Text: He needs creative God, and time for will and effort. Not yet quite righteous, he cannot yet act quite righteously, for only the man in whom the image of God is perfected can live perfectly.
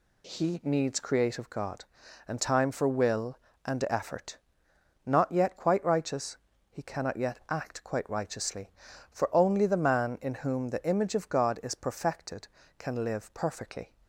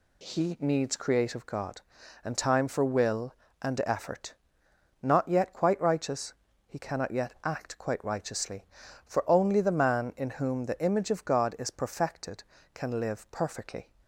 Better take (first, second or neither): neither